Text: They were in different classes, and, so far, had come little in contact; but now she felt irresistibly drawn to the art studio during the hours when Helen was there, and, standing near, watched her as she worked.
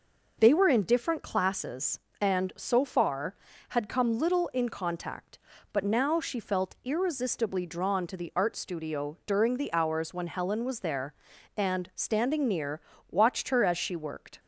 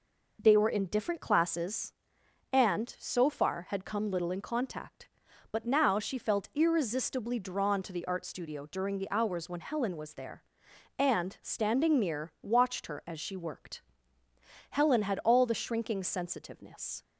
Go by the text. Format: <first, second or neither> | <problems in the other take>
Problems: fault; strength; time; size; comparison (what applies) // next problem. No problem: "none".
first | goes on to say "Helen had all the shrinking sensitiveness"; strong; from 14.7 s on; 2.3 s long